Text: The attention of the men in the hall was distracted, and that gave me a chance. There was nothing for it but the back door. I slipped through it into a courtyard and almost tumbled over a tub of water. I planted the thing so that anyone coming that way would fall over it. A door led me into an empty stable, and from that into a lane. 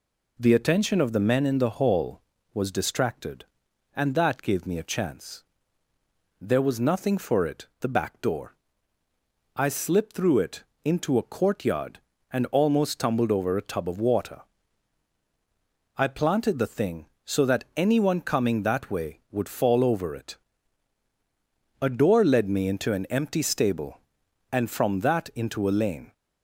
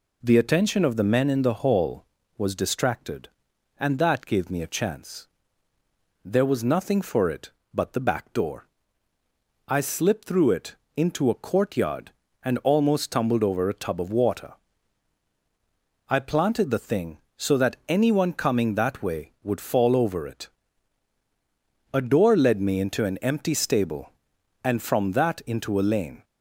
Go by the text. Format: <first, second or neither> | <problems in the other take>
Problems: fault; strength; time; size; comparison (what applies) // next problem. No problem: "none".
second | skips "but"; at 7.7 s // pauses between "it" and "into"; slight; at 10.6 s; 0.20 s long; slight in the second